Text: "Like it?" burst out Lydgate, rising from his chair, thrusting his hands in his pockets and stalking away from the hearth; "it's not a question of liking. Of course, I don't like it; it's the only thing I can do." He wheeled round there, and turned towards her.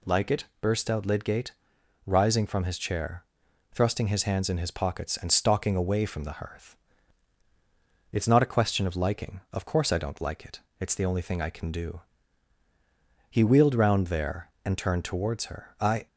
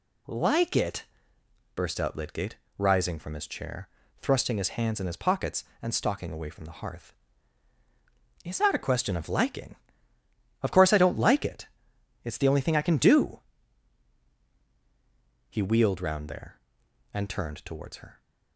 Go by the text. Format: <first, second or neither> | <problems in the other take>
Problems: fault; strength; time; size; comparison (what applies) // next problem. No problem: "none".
second | goes on to say "I"; slight; from 15.7 s on; 0.28 s long